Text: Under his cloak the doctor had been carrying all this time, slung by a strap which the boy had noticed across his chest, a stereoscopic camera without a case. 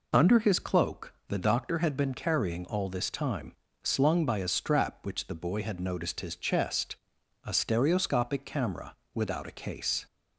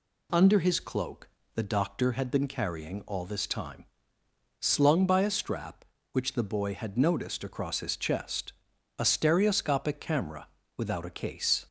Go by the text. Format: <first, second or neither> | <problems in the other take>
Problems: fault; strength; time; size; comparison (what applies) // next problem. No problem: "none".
second | pauses between "cloak" and "the"; slight; at 1.1 s; 0.16 s long; slight in the second // skips "across"; at 6.1 s // pauses between "camera" and "without"; slight; at 8.9 s; 0.22 s long; slight in the second